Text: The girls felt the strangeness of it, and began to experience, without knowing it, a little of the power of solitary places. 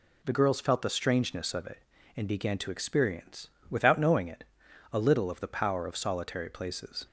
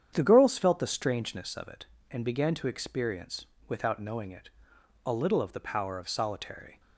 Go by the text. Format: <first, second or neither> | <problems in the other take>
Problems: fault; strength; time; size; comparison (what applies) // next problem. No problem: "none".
first | starts louder than the rest; strong; until 1.1 s; 8.5 dB // stops before "places"; at 6.7 s